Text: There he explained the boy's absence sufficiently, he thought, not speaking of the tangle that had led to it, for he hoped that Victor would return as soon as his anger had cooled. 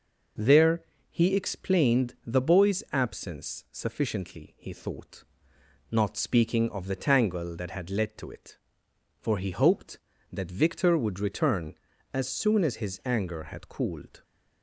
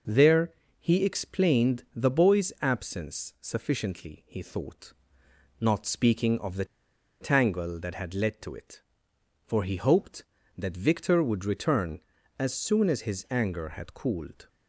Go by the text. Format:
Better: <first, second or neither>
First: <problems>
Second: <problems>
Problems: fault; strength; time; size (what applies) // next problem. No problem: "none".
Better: first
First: pauses between "There" and "he"; slight; at 0.8 s; 0.26 s long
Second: pauses between "There" and "he"; slight; at 0.5 s; 0.26 s long // pauses between "the" and "tangle"; noticeable; at 6.6 s; 0.56 s long